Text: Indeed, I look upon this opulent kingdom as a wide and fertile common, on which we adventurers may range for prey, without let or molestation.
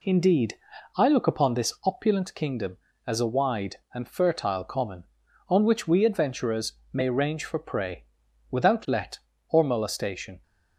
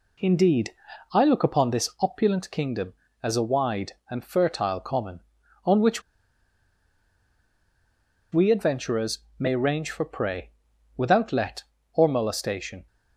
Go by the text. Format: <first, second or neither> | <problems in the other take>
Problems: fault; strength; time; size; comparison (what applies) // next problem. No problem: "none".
first | pauses between "which" and "we"; strong; at 6.0 s; 2.3 s long // pauses between "adventurers" and "may"; slight; at 9.1 s; 0.20 s long; slight in the first